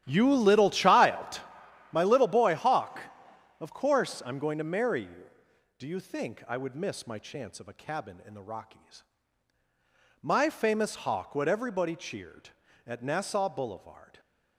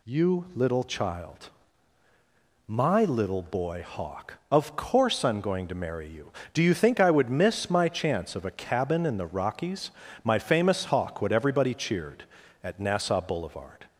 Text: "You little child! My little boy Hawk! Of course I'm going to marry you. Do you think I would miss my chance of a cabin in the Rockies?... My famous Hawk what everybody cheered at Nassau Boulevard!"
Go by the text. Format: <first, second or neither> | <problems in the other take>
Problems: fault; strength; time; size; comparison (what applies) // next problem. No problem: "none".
second | gets quieter; strong; throughout; 14 dB